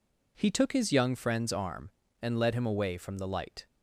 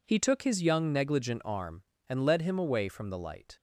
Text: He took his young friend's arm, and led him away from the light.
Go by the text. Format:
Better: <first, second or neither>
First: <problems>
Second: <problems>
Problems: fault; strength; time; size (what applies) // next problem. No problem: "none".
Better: first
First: none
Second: says "negligent" for "friend's"; at 0.9 s